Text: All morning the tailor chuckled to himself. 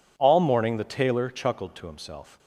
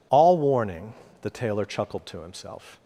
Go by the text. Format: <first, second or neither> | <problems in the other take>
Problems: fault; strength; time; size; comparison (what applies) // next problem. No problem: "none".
first | says "warning" for "morning"; at 0.3 s